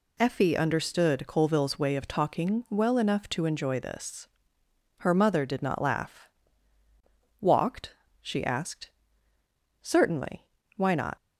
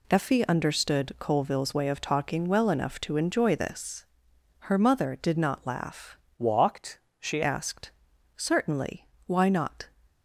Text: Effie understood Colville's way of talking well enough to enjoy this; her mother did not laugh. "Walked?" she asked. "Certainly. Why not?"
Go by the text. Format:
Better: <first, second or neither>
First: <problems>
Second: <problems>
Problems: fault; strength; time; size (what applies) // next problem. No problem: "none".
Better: first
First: none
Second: changes voice from "Walked" to "she"; from 6.3 to 7.4 s; 1.1 s long